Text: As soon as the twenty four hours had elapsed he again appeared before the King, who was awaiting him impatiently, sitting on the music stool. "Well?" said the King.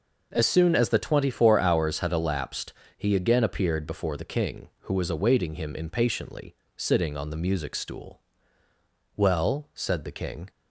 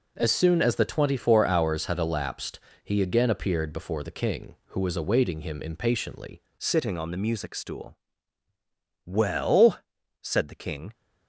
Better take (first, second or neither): first